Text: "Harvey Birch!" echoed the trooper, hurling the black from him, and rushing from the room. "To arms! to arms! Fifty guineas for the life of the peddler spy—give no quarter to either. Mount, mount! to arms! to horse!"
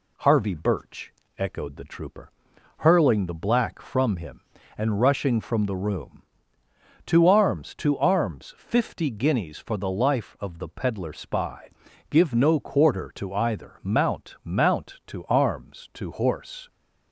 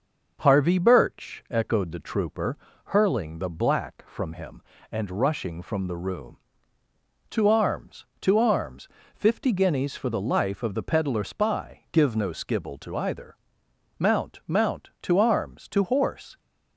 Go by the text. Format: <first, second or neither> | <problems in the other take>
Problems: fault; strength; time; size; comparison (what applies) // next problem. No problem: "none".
first | starts louder than the rest; until 1.4 s; 6 dB // says "skibble" for "quarter"; at 12.3 s